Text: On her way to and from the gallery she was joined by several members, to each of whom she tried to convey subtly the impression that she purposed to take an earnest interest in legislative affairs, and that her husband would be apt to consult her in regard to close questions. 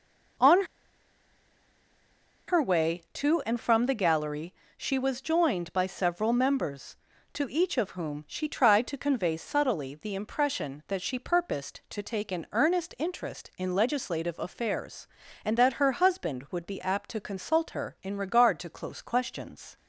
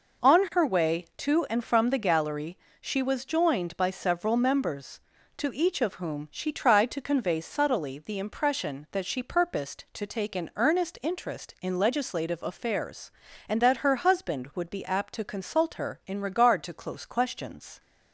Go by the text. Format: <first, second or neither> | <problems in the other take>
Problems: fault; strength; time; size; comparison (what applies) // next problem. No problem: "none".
second | pauses between "On" and "her"; strong; at 0.6 s; 1.8 s long // pauses between "gallery" and "she"; slight; at 4.5 s; 0.24 s long; slight in the second